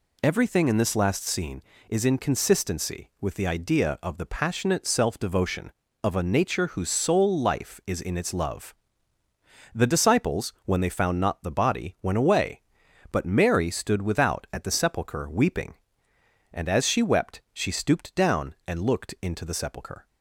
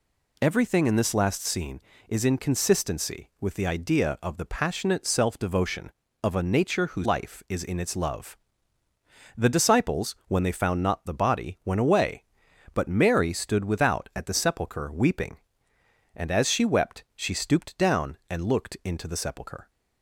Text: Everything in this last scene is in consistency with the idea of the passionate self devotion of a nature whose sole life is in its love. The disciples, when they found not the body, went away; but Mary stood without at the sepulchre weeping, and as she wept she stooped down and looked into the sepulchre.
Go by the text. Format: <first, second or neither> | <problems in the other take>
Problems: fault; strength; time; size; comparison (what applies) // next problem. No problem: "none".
first | skips "sole"; at 7.0 s